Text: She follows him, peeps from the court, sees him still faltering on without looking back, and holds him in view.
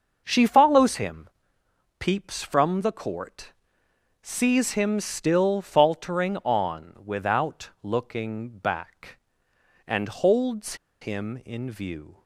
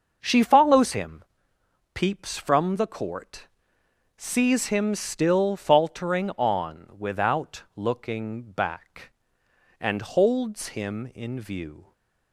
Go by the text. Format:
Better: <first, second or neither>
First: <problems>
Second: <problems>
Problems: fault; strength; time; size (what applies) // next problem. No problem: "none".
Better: second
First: starts louder than the rest; until 1.2 s; 6.5 dB // pauses between "holds" and "him"; slight; at 10.7 s; 0.26 s long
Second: starts louder than the rest; until 1.2 s; 6.5 dB